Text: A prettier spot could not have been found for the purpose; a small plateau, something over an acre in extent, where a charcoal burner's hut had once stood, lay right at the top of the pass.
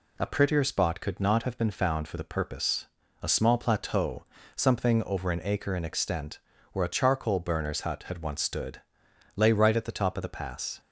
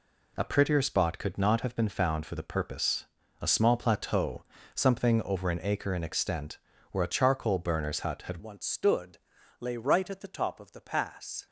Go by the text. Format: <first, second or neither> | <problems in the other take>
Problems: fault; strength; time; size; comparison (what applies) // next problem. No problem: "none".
first | changes voice at "once"; from 8.4 s on; 3.0 s long